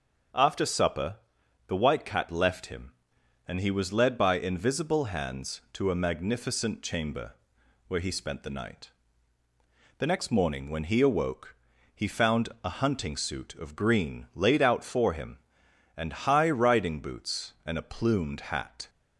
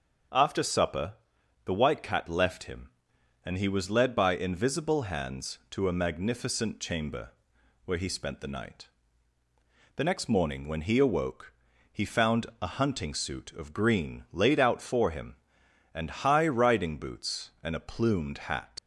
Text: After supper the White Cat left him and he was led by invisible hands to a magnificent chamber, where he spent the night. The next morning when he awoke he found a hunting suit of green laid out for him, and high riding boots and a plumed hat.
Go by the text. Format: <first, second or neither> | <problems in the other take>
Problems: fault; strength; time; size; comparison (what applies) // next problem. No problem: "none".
first | starts louder than the rest; until 1.8 s; 6.5 dB; also in the first // pauses between "supper" and "the"; noticeable; at 1.1 s; 0.52 s long; noticeable in the first // pauses between "awoke" and "he"; at 11.5 s; 0.40 s long; also in the first // leaves "hat" unfinished; at 18.7 s; 80 ms